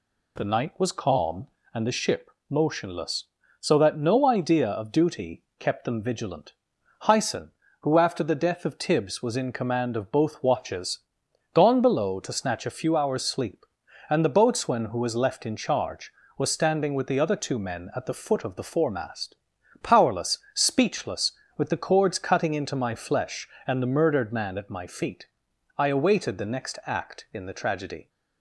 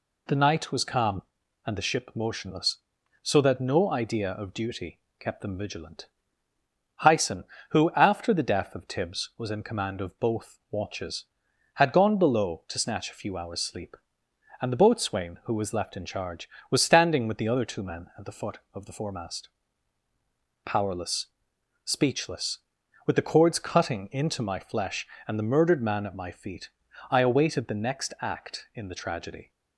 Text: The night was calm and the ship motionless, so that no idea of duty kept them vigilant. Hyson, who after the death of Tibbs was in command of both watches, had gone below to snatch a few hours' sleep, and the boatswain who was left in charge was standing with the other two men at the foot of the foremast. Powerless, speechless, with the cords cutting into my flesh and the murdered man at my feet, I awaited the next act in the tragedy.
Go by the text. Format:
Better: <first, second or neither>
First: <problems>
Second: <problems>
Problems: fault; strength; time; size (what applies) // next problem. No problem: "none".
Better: second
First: pauses between "ship" and "motionless"; slight; at 2.2 s; 0.20 s long // pauses between "duty" and "kept"; slight; at 5.4 s; 0.16 s long // skips "had"; at 11.2 s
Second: pauses between "duty" and "kept"; slight; at 4.9 s; 0.22 s long